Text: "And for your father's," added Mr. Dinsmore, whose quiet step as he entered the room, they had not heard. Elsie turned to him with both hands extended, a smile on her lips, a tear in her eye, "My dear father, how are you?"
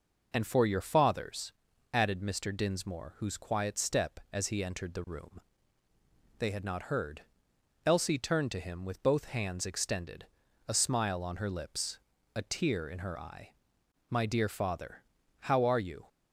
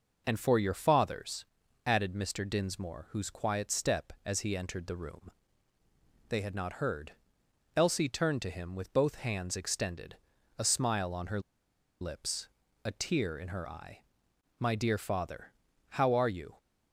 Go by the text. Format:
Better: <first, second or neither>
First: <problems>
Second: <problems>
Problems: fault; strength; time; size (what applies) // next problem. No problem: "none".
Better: first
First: none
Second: pauses between "her" and "lips"; noticeable; at 11.4 s; 0.60 s long